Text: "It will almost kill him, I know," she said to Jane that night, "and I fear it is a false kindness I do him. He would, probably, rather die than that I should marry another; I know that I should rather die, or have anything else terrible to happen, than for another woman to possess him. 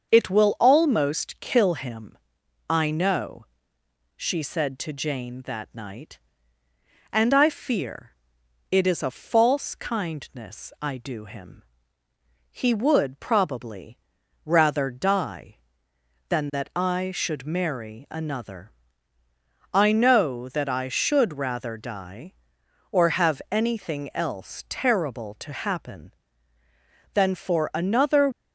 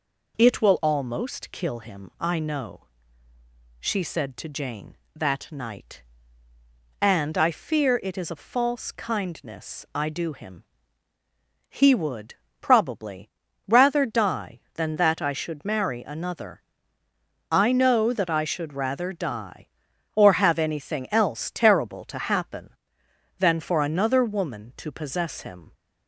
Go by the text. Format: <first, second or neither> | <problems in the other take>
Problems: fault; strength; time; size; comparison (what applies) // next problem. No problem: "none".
second | starts louder than the rest; until 1.1 s; 6.5 dB // pauses between "fear" and "it"; noticeable; at 8.1 s; 0.58 s long // stops before "woman to possess him"; at 28.3 s